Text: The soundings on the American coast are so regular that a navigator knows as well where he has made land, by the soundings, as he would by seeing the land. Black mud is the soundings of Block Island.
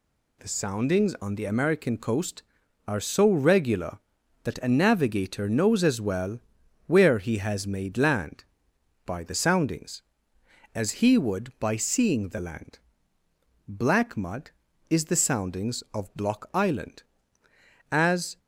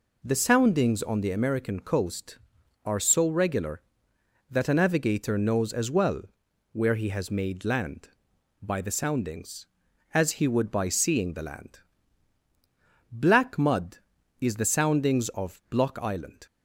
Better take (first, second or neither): second